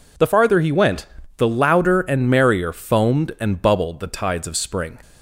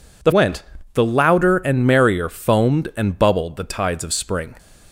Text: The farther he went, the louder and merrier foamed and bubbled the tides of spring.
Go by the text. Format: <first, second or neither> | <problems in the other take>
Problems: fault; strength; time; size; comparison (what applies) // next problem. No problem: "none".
first | skips "farther he"; at 0.3 s